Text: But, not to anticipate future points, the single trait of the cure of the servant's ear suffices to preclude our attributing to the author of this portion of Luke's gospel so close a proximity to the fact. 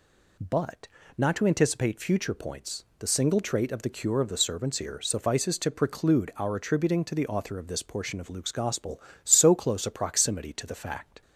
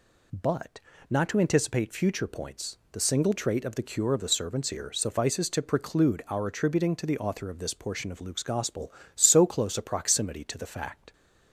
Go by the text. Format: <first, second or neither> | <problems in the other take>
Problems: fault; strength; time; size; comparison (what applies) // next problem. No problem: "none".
neither | none